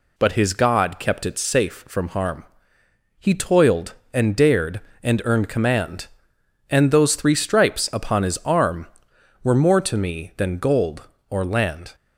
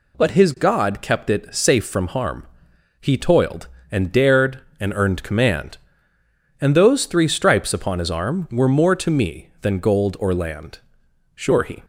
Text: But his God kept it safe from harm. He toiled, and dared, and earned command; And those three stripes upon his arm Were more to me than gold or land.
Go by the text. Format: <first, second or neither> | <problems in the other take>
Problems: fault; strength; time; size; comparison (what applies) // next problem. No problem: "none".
first | goes on to say "Sure he"; slight; from 11.3 s on; 0.48 s long